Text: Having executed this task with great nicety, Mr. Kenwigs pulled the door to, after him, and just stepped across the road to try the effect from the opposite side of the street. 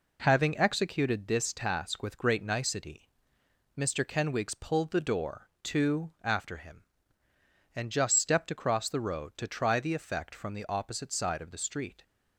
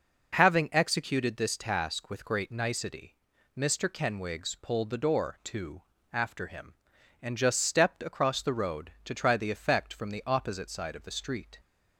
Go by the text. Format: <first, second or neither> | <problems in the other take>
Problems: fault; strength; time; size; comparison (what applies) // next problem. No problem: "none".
neither | none